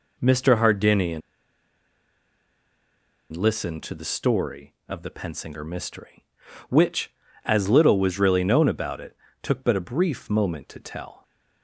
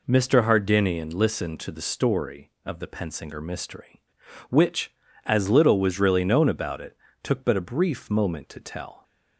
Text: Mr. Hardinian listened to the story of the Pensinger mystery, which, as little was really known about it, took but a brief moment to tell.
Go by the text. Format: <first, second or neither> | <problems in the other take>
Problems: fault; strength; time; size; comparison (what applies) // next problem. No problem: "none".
second | pauses between "Hardinian" and "listened"; strong; at 1.2 s; 2.1 s long